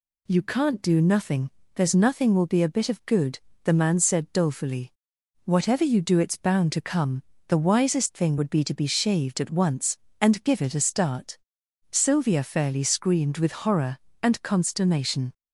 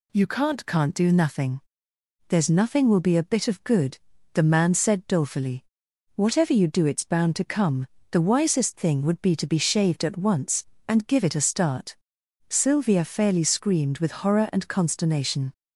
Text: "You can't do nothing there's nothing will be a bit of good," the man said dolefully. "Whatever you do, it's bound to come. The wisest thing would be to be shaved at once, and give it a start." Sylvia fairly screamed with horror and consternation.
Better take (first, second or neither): first